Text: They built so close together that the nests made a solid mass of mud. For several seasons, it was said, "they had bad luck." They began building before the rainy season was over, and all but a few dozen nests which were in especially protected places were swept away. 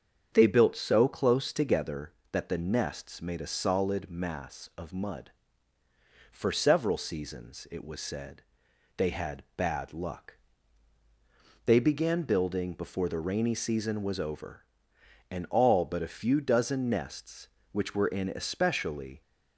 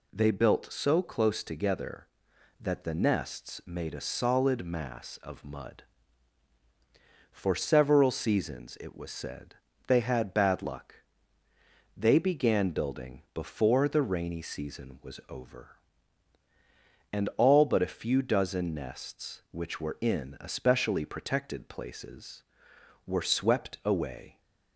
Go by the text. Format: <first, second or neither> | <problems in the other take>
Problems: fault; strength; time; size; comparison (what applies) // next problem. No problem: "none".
second | starts louder than the rest; strong; until 1.3 s; 7.5 dB // stops before "protected places were swept away"; at 19.2 s